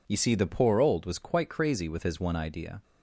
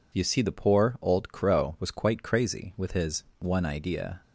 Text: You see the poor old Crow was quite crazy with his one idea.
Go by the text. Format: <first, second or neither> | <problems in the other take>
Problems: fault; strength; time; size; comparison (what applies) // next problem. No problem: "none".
second | skips "Crow"; at 1.0 s